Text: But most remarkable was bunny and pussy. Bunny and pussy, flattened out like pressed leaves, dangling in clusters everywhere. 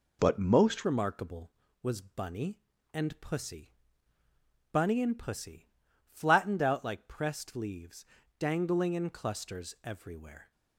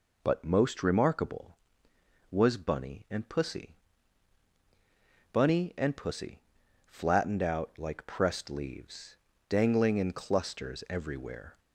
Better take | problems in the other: second | changes voice at "remarkable"; from 0.8 s on; 9.7 s long

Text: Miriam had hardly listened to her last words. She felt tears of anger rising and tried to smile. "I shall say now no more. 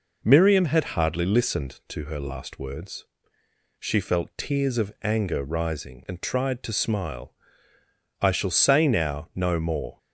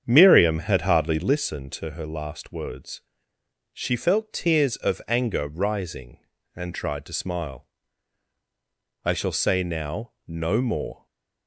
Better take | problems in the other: first | starts louder than the rest; strong; until 1.4 s; 8 dB // stays silent after the last word; slight; from 10.9 s on; 0.5 s long

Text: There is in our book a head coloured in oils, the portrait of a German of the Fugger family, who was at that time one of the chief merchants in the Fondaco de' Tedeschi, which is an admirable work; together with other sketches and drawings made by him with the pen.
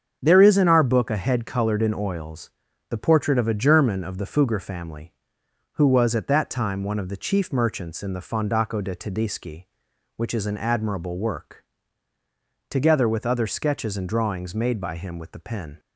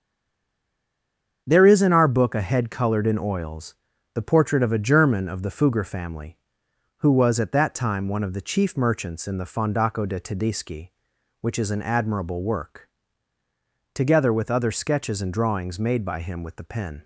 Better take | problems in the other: first | stays silent before the first word; noticeable; until 1.4 s; 1.4 s long // starts louder than the rest; strong; until 2.4 s; 7 dB; strong in the first

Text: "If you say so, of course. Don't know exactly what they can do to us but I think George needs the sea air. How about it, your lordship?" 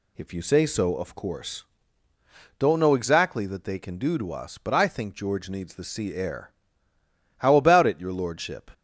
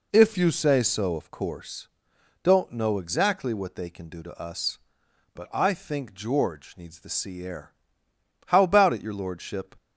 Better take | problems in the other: second | says "that" for "what"; at 3.4 s

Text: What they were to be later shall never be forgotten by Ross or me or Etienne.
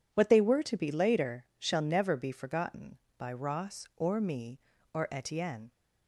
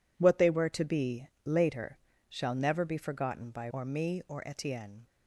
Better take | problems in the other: first | pauses between "be" and "later"; slight; at 1.2 s; 0.18 s long // pauses between "later" and "shall"; slight; at 1.9 s; 0.30 s long // skips "Ross"; at 3.6 s

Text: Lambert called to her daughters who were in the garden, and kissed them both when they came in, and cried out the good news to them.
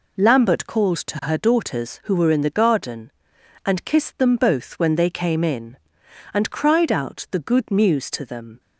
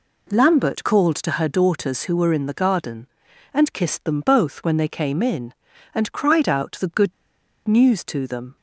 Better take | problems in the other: first | pauses between "good" and "news"; noticeable; at 7.1 s; 0.54 s long

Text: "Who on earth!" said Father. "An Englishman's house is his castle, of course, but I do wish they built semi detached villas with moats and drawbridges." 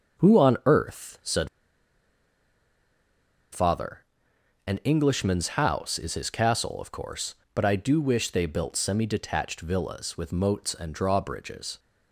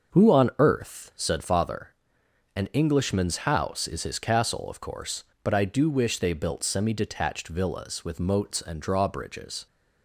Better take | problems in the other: second | starts louder than the rest; until 1.3 s; 6.5 dB; also in the second // pauses between "said" and "Father"; strong; at 1.4 s; 2.0 s long

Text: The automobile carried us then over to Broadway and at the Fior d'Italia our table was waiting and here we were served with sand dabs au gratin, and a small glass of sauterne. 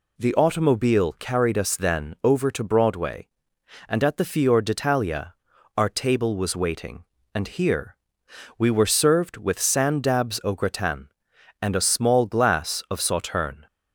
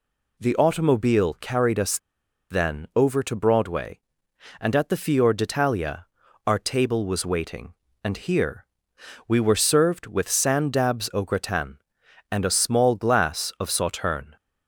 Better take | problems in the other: first | pauses between "us" and "then"; noticeable; at 1.9 s; 0.53 s long // pauses between "d'Italia" and "our"; at 6.0 s; 0.40 s long; also in the first // pauses between "here" and "we"; noticeable; at 8.6 s; 0.62 s long; noticeable in the first

